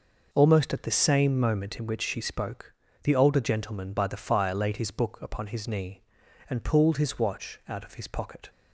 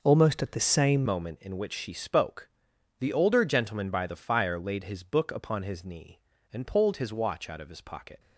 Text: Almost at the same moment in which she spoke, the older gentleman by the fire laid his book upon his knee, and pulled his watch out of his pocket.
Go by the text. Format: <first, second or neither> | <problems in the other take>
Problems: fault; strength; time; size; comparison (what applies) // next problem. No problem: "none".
first | changes voice at "moment"; from 1.0 s on; 7.1 s long